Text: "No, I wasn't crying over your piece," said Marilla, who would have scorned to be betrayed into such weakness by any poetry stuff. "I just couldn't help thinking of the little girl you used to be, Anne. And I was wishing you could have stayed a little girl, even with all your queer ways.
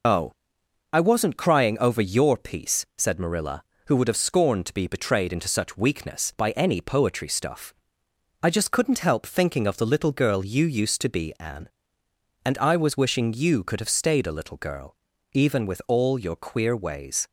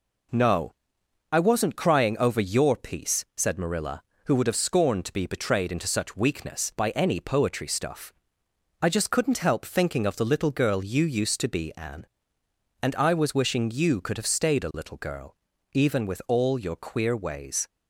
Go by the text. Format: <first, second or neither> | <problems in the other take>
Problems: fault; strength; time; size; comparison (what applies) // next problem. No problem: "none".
second | loses the start of "No"; at 0.0 s; 135 ms